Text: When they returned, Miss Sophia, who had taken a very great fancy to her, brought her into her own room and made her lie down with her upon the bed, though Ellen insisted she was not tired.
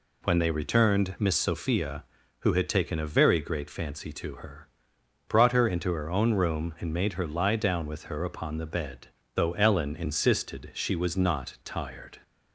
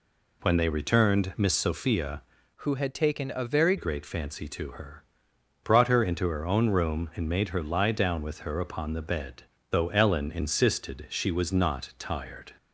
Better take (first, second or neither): first